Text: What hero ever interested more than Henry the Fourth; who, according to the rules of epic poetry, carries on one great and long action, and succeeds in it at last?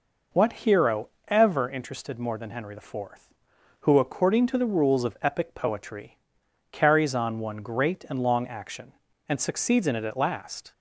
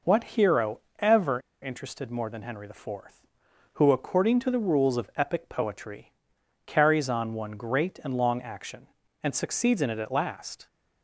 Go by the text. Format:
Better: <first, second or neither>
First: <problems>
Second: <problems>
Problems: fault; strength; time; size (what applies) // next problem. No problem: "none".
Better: first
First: pauses between "hero" and "ever"; slight; at 1.0 s; 0.20 s long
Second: pauses between "hero" and "ever"; slight; at 0.7 s; 0.20 s long // pauses between "ever" and "interested"; slight; at 1.3 s; 0.22 s long